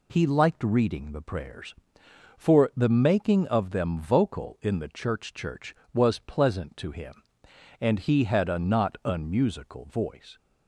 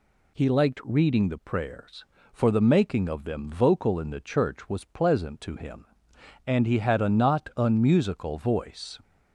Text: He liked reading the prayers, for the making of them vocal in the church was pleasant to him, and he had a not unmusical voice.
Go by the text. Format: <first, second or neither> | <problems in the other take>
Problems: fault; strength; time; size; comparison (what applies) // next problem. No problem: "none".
second | says "church" twice; at 5.3 s